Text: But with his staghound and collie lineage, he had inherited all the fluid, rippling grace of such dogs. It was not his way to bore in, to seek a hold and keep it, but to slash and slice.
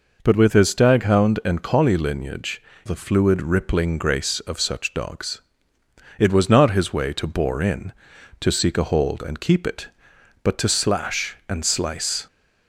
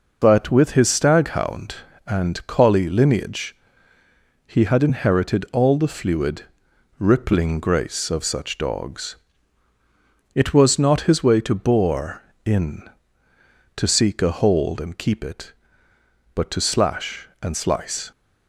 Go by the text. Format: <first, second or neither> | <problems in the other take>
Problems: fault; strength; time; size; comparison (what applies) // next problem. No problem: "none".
second | skips "he had inherited all"; at 2.7 s